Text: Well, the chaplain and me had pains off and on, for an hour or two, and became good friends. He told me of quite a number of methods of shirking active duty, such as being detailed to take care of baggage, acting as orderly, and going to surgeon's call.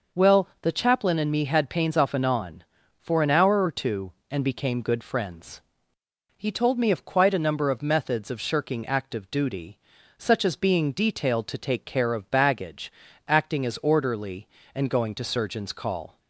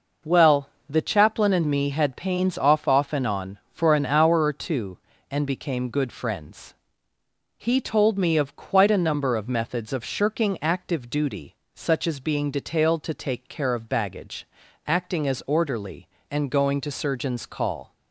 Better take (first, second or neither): first